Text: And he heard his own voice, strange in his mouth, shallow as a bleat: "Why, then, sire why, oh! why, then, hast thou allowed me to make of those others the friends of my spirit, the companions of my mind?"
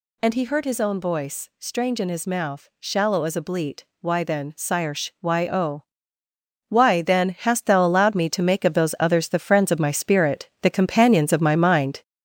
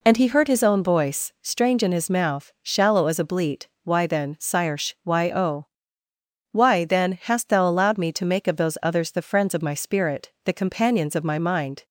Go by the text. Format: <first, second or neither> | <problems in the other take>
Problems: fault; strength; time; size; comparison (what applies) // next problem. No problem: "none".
second | gets louder; noticeable; throughout; 5.5 dB // pauses between "sire" and "why"; slight; at 4.9 s; 0.26 s long; slight in the second